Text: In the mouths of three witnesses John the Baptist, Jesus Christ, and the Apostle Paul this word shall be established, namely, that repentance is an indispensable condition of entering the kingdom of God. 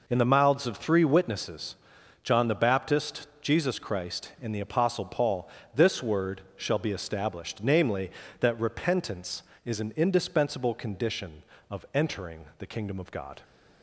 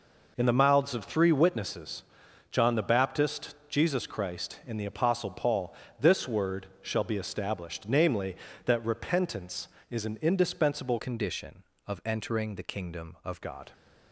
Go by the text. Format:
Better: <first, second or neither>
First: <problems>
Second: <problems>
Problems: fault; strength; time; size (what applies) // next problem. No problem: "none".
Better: first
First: pauses between "witnesses" and "John"; noticeable; at 1.7 s; 0.48 s long // pauses between "Paul" and "this"; slight; at 5.4 s; 0.28 s long // pauses between "word" and "shall"; slight; at 6.4 s; 0.16 s long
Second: pauses between "witnesses" and "John"; noticeable; at 2.0 s; 0.48 s long // pauses between "Paul" and "this"; slight; at 5.7 s; 0.28 s long // pauses between "word" and "shall"; slight; at 6.6 s; 0.16 s long // changes voice from "condition" to "of"; from 10.9 to 13.4 s; 2.5 s long